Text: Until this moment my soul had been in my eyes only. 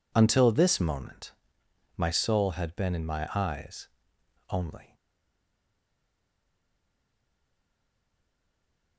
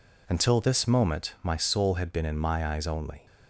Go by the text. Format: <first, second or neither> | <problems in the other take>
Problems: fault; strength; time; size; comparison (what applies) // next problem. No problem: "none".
second | pauses between "moment" and "my"; noticeable; at 1.3 s; 0.66 s long // pauses between "eyes" and "only"; noticeable; at 3.8 s; 0.62 s long // stays silent after the last word; strong; from 4.9 s on; 4.0 s long